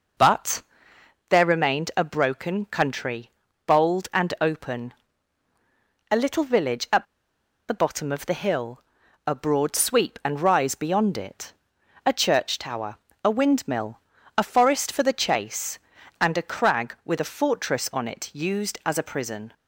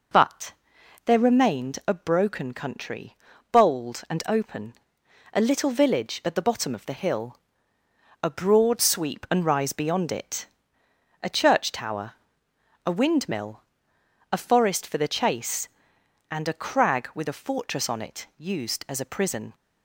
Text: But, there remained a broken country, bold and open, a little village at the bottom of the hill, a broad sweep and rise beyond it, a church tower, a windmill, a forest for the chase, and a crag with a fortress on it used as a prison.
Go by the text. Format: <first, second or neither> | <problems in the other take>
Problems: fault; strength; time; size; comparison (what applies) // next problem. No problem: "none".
second | pauses between "at" and "the"; noticeable; at 7.0 s; 0.64 s long